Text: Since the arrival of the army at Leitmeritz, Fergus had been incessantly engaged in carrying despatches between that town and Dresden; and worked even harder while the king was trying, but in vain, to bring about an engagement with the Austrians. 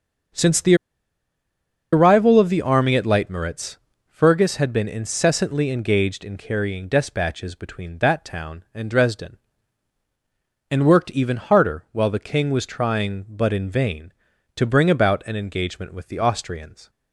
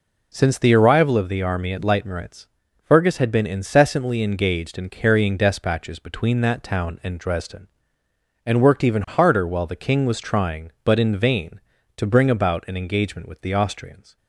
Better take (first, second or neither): second